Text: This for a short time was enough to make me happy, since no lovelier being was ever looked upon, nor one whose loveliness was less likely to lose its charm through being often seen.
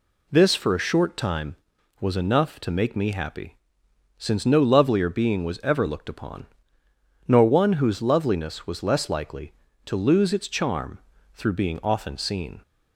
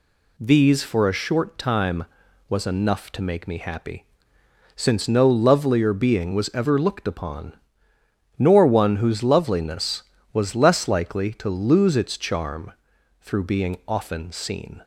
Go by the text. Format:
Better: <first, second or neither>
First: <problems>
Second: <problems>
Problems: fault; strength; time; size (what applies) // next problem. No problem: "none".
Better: first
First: pauses between "charm" and "through"; slight; at 10.9 s; 0.36 s long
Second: says "These" for "This"; at 0.3 s // pauses between "charm" and "through"; noticeable; at 12.7 s; 0.48 s long